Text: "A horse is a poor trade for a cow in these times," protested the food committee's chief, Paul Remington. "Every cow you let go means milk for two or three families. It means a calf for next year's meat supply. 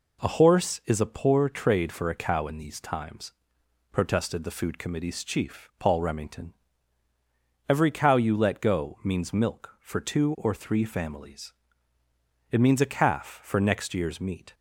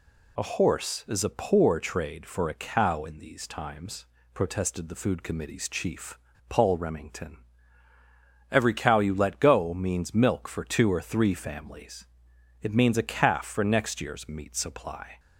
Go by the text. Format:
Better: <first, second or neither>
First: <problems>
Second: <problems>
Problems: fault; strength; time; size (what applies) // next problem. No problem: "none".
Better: second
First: stops before "supply"; at 14.5 s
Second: none